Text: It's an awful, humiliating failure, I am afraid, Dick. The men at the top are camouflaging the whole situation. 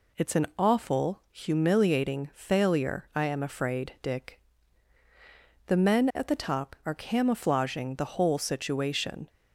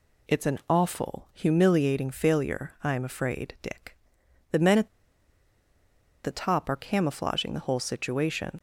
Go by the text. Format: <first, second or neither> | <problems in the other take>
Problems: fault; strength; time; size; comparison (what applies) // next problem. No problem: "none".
first | pauses between "at" and "the"; strong; at 4.8 s; 1.3 s long